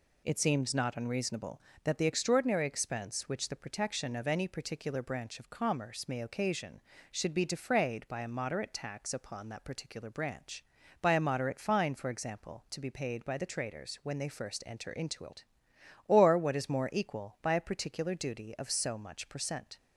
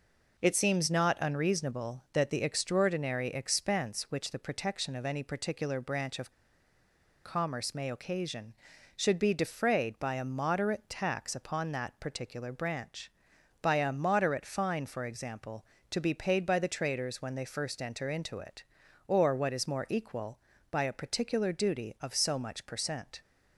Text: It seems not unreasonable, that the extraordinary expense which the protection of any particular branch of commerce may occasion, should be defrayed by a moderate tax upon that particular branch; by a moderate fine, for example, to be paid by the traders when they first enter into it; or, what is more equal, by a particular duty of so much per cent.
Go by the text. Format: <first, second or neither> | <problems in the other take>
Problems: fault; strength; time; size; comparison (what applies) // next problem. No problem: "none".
first | pauses between "of" and "commerce"; noticeable; at 6.3 s; 0.93 s long